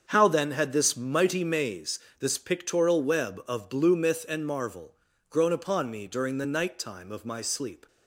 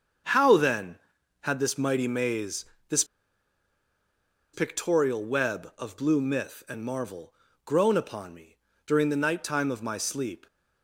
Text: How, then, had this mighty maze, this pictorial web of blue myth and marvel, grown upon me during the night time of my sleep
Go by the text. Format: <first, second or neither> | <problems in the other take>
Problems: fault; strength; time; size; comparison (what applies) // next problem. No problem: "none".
first | starts louder than the rest; strong; until 1.7 s; 7 dB; also in the first // pauses between "this" and "pictorial"; strong; at 3.0 s; 1.4 s long // pauses between "me" and "during"; slight; at 8.5 s; 0.30 s long